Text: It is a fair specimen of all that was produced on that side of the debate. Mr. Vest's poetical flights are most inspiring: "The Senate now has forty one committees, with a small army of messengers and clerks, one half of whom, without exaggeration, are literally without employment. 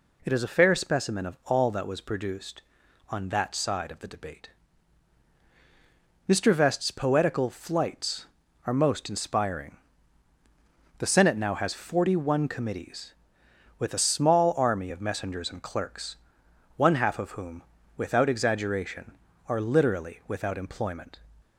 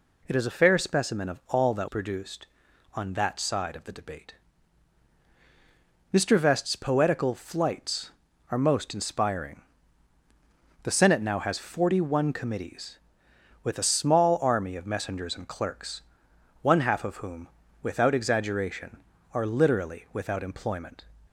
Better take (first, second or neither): first